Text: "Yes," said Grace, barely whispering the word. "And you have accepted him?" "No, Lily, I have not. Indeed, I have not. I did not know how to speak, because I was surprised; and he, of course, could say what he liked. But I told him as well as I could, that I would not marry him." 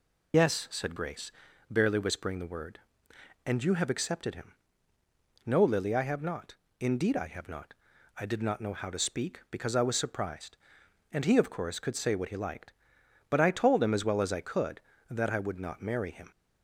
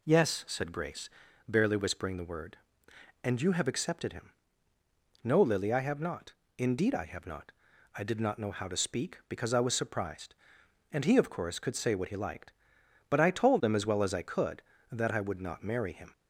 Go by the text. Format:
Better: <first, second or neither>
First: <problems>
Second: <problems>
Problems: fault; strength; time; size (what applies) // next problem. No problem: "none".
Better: second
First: loses the start of "Yes"; at 0.3 s; 65 ms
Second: none